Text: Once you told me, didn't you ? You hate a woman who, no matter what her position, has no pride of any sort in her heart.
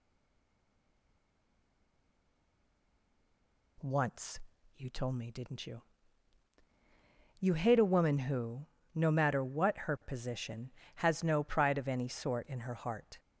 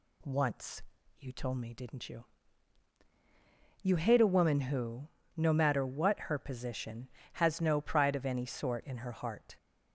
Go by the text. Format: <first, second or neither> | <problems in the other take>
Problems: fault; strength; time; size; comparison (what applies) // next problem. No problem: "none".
second | stays silent before the first word; strong; until 3.7 s; 3.7 s long // pauses between "Once" and "you"; slight; at 4.4 s; 0.34 s long; slight in the second